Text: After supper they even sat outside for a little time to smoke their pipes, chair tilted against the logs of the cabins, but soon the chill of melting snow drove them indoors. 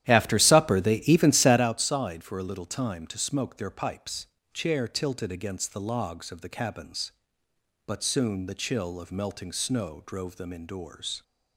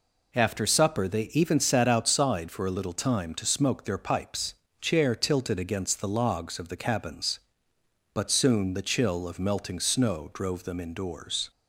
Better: second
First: starts louder than the rest; strong; until 1.7 s; 12 dB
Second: none

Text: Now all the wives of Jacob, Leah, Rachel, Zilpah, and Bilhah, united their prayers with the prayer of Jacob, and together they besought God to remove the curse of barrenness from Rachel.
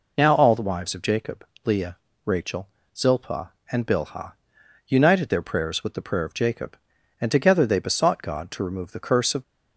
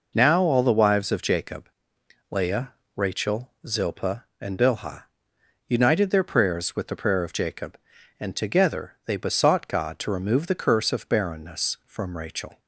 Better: second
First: stops before "barrenness from Rachel"; at 9.4 s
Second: none

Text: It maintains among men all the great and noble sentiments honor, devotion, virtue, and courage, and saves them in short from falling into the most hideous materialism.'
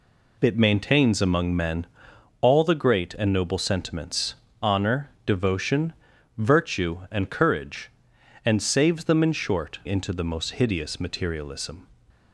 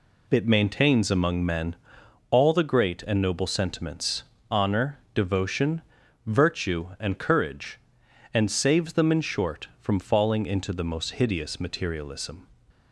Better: second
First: pauses between "men" and "all"; noticeable; at 1.8 s; 0.54 s long // pauses between "sentiments" and "honor"; slight; at 4.3 s; 0.26 s long // skips "from falling"; at 9.8 s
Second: pauses between "men" and "all"; noticeable; at 1.7 s; 0.54 s long // pauses between "sentiments" and "honor"; slight; at 4.2 s; 0.26 s long

